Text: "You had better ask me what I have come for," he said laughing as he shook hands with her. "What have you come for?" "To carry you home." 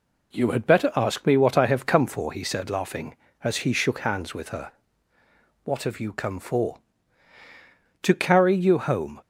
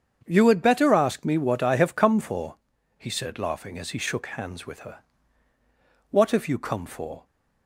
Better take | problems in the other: first | starts louder than the rest; strong; until 1.2 s; 7.5 dB // stops before "To carry you home"; at 7.2 s

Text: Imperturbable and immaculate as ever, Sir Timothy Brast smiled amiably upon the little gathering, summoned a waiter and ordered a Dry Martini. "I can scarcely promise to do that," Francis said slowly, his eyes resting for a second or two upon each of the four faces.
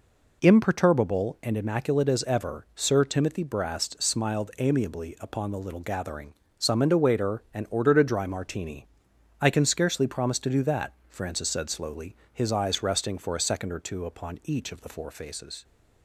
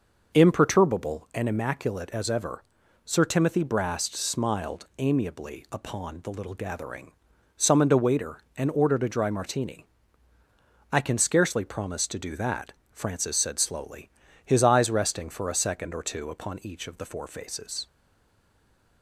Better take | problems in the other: first | stays silent after the last word; from 17.8 s on; 1.2 s long

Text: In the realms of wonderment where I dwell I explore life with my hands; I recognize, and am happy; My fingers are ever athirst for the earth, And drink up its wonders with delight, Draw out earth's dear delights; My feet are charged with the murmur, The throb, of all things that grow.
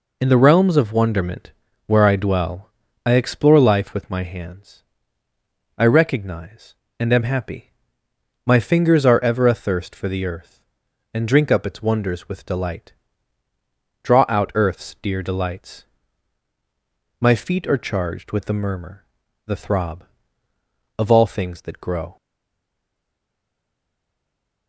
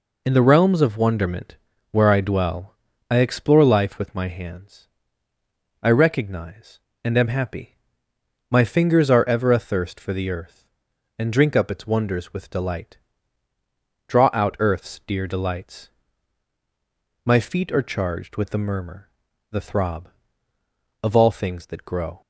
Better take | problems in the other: second | pauses between "wonderment" and "where"; slight; at 1.5 s; 0.34 s long; slight in the second // pauses between "dwell" and "I"; slight; at 2.7 s; 0.36 s long; slight in the second // stays silent after the last word; strong; from 22.1 s on; 2.5 s long

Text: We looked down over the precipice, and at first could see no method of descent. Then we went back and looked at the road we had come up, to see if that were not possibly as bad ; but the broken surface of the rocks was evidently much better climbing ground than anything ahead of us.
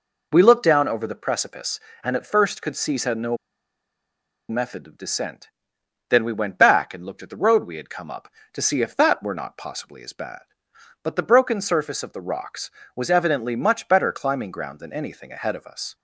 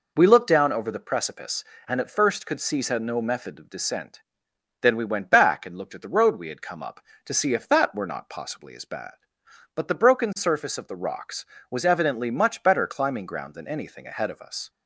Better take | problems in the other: second | pauses between "see" and "no"; slight; at 2.9 s; 0.16 s long; slight in the second // pauses between "no" and "method"; at 3.3 s; 1.1 s long

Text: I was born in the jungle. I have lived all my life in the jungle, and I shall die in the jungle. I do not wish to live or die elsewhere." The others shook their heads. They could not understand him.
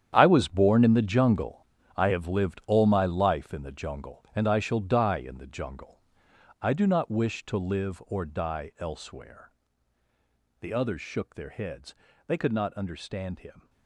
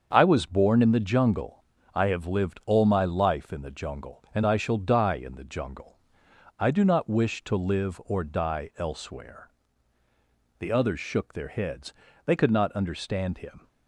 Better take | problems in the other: second | gets quieter; strong; throughout; 13.5 dB // starts louder than the rest; strong; until 1.1 s; 9.5 dB; also in the second

